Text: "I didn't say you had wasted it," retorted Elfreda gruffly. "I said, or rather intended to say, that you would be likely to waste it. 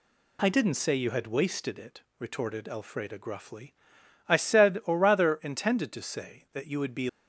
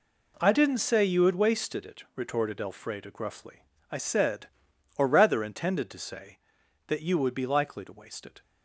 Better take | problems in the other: second | stops before "likely to waste it"; at 7.0 s

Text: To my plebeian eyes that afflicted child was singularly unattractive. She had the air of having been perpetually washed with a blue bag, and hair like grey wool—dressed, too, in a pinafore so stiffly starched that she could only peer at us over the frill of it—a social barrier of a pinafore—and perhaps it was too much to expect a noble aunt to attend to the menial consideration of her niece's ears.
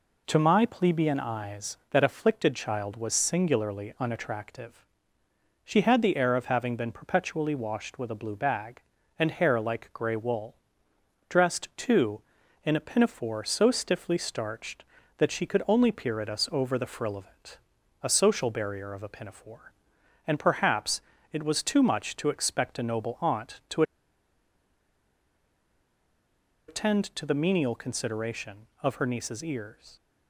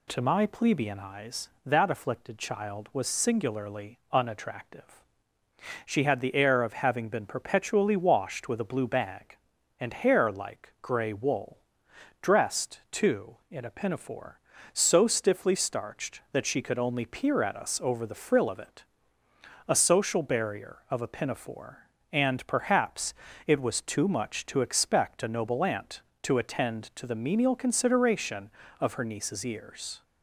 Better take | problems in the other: second | pauses between "perhaps" and "it"; slight; at 21.0 s; 0.32 s long; slight in the second // pauses between "to" and "attend"; strong; at 23.8 s; 2.8 s long

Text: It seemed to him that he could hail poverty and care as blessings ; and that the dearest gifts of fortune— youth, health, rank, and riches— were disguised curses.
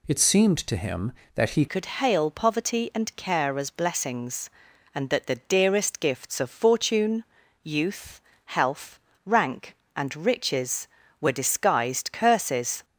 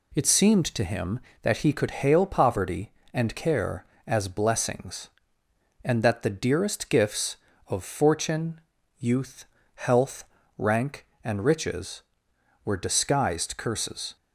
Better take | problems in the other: second | changes voice at "could"; from 1.6 s on; 11.2 s long

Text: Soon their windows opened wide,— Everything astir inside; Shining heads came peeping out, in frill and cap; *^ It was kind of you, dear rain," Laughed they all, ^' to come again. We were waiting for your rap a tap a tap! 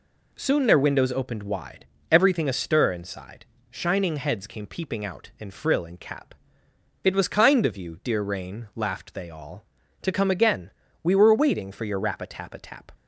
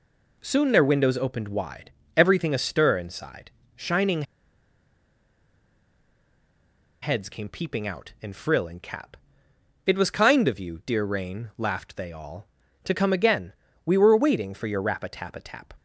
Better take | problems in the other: first | pauses between "Shining" and "heads"; strong; at 4.2 s; 2.7 s long

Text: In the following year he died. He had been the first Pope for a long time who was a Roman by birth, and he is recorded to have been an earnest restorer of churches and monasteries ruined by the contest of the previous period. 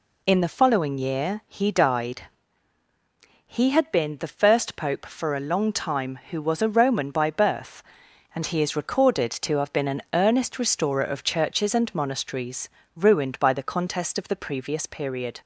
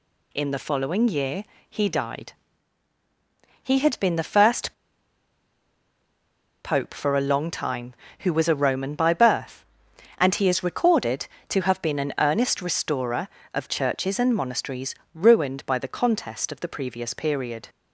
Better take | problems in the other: first | pauses between "year" and "he"; slight; at 1.4 s; 0.26 s long // pauses between "first" and "Pope"; strong; at 4.7 s; 1.9 s long // pauses between "monasteries" and "ruined"; slight; at 14.9 s; 0.22 s long; slight in the first

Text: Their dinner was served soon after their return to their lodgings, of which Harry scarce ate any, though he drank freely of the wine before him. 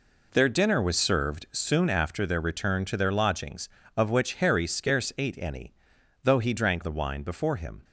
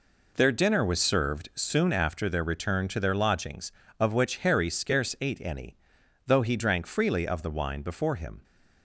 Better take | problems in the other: second | skips "freely of"; at 6.8 s

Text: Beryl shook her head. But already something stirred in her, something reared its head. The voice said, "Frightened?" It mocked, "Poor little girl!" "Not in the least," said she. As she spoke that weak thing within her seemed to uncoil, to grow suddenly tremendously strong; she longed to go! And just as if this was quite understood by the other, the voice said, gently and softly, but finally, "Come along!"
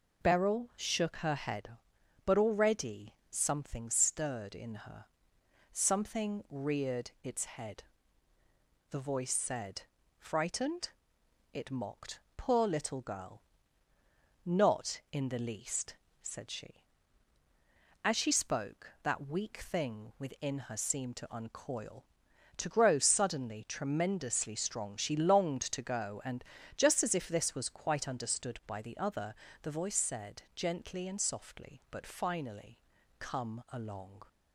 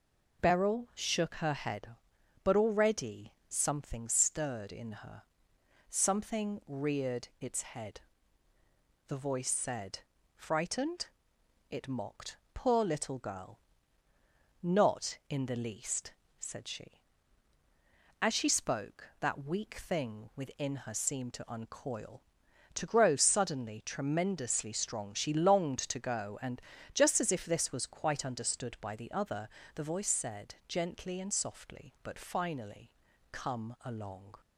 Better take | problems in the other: neither | pauses between "already" and "something"; slight; the same in both // pauses between "And" and "just"; slight; the same in both

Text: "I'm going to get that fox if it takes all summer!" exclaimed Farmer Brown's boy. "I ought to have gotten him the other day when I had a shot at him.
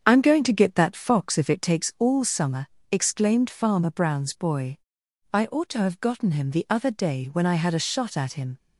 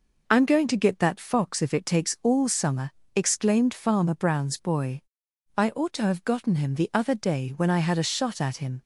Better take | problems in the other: second | starts louder than the rest; strong; until 1.7 s; 7.5 dB

